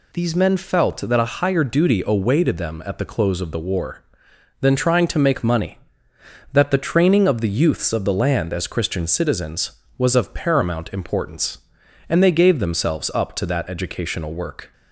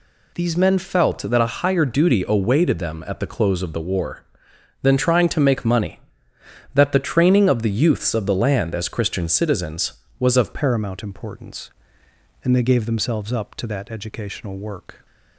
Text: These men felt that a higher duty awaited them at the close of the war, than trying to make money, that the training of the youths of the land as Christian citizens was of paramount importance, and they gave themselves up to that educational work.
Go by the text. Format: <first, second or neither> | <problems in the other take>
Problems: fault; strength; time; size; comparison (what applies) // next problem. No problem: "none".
first | changes voice at "paramount"; from 10.5 s on; 4.5 s long